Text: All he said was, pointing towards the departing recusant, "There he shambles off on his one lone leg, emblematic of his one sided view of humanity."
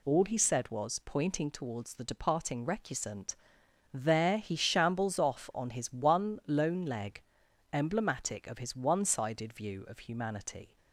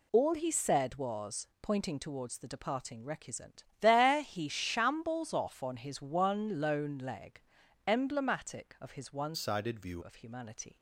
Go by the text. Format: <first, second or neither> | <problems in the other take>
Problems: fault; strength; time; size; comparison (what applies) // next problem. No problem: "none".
first | changes voice from "sided" to "view"; from 9.3 to 10.0 s; 0.7 s long